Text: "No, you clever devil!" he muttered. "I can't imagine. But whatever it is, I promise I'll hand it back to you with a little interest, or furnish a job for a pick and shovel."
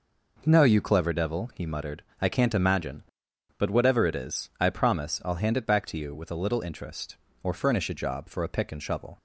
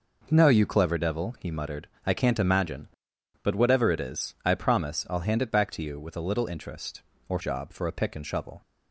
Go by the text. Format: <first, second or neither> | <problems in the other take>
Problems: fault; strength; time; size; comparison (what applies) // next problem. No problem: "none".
first | skips "furnish a"; at 7.4 s